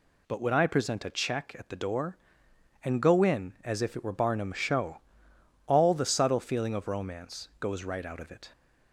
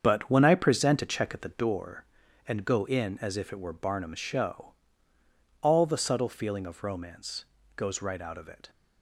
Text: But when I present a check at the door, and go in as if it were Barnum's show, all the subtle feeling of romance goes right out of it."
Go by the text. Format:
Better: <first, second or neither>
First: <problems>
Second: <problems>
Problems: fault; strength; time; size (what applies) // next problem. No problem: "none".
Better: first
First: none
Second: starts louder than the rest; strong; until 1.7 s; 7.5 dB // pauses between "romance" and "goes"; slight; at 7.4 s; 0.32 s long